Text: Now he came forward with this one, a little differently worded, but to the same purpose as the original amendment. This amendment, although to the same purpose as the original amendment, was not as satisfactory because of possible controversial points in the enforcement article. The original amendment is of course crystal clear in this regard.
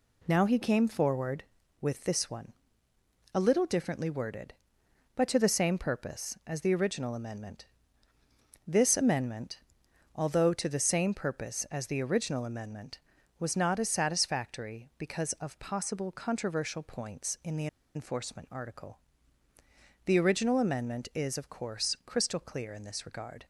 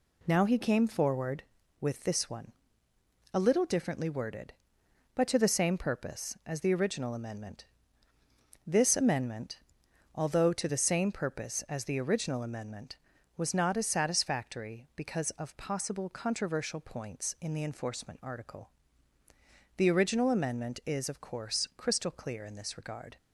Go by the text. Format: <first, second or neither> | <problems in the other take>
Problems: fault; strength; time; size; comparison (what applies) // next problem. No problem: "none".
second | pauses between "the" and "enforcement"; slight; at 17.6 s; 0.28 s long